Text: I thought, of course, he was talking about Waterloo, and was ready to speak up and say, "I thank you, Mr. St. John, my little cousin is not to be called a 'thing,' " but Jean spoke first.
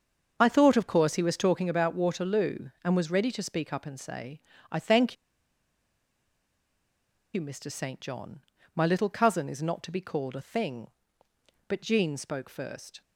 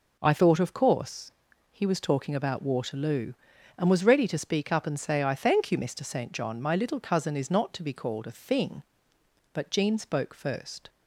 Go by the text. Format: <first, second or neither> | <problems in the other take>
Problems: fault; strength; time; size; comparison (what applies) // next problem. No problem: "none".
second | starts louder than the rest; until 1.3 s; 7 dB // pauses between "thank" and "you"; strong; at 5.1 s; 2.1 s long